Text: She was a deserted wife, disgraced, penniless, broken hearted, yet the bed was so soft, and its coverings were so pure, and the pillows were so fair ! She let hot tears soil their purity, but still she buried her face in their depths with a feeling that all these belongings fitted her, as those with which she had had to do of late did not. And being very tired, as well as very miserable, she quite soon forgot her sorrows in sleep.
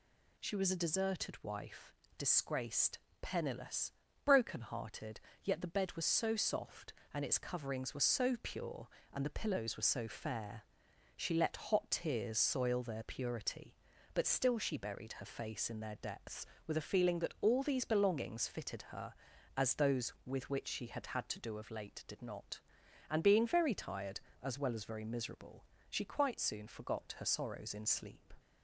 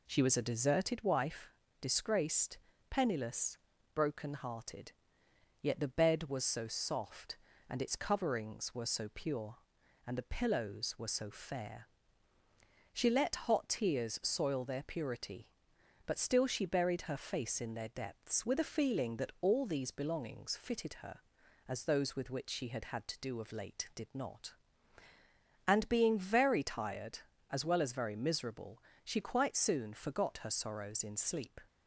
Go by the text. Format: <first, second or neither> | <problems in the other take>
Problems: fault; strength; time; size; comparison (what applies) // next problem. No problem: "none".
first | starts louder than the rest; slight; until 1.0 s; 2.5 dB